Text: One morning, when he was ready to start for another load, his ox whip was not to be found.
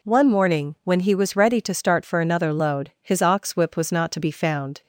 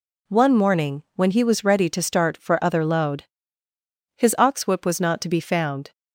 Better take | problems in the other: first | says "other" for "another"; at 2.6 s

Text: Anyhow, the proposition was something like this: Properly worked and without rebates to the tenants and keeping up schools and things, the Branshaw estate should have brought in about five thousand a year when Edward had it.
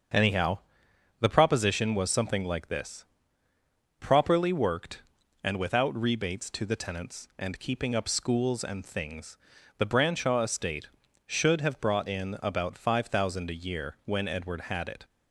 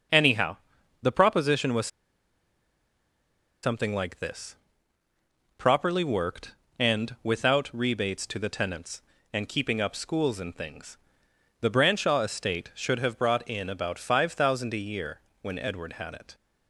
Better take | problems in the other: first | starts louder than the rest; until 1.5 s; 6.5 dB; also in the first // pauses between "was" and "something"; strong; at 1.8 s; 1.7 s long // pauses between "year" and "when"; slight; at 15.2 s; 0.20 s long

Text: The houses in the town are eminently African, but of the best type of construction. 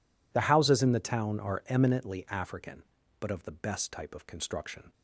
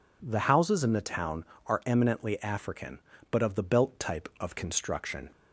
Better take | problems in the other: first | says "belt" for "best"; at 3.6 s

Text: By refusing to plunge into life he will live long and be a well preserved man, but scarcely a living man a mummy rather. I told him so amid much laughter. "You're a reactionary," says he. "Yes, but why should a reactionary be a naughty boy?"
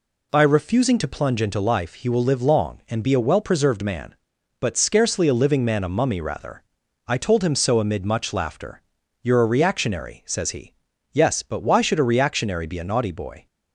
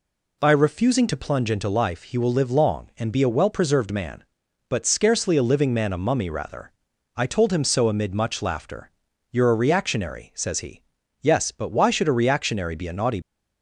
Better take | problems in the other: first | stops before "boy"; at 13.2 s

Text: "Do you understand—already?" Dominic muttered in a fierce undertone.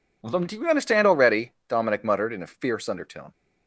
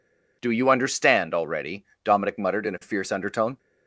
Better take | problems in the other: neither | none

